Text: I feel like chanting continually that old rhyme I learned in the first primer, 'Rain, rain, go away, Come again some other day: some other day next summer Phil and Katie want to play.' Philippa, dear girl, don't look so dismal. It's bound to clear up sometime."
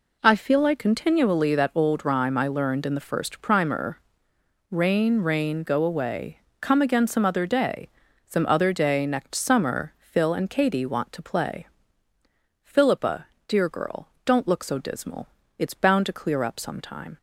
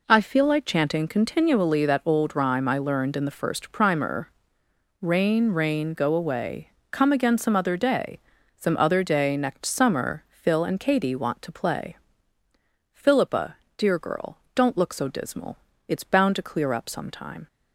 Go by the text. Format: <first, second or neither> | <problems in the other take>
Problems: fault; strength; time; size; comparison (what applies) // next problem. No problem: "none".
second | skips "chanting"; at 0.7 s